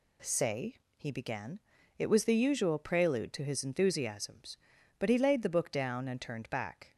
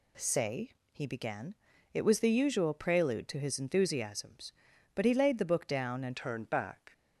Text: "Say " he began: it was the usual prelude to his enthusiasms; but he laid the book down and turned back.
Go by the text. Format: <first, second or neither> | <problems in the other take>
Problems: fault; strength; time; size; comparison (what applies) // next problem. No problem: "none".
first | changes voice at "turned"; from 6.1 s on; 0.8 s long